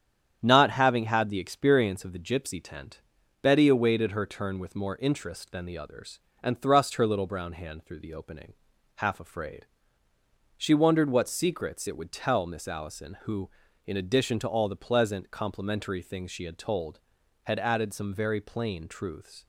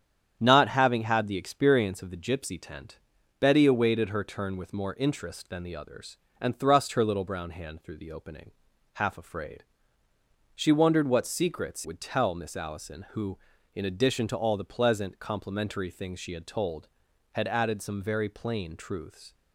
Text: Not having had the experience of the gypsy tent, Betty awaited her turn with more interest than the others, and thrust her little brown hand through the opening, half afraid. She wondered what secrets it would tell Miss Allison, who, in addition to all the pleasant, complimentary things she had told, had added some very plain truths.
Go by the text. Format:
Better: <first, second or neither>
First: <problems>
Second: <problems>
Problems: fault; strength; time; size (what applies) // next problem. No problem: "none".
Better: first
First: starts louder than the rest; strong; until 1.4 s; 9 dB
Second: starts louder than the rest; strong; until 1.4 s; 9 dB // skips "it"; at 11.8 s